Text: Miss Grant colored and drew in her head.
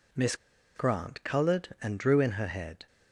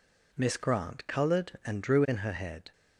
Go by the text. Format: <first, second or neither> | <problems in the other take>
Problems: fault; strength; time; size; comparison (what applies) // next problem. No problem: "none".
second | pauses between "Miss" and "Grant"; at 0.3 s; 0.40 s long